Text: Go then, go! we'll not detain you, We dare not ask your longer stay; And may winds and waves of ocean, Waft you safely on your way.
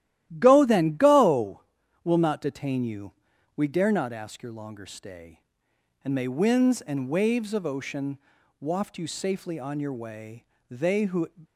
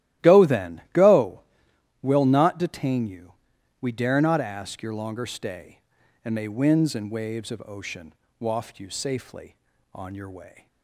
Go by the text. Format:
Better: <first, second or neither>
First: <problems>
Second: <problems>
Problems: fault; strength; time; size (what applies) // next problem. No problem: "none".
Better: second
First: starts louder than the rest; strong; until 1.3 s; 13.5 dB // goes on to say "They who"; from 10.6 s on; 0.60 s long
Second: starts louder than the rest; strong; until 1.3 s; 14.5 dB